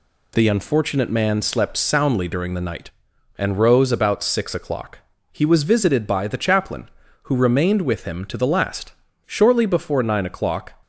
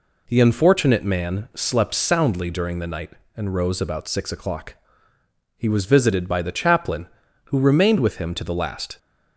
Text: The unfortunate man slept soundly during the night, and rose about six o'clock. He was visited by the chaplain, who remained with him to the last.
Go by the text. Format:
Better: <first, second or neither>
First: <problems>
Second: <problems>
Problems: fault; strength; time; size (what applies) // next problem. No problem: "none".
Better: second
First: goes on to say "Shortly before nine o'clock"; from 9.2 s on; 1.4 s long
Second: none